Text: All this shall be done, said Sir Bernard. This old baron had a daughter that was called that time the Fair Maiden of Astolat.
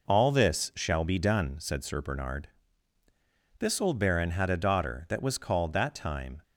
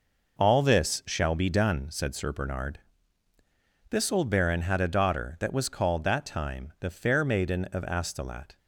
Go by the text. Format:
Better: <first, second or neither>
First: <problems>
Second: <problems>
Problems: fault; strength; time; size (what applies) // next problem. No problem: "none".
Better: second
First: stops before "the Fair Maiden of Astolat"; at 6.4 s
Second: none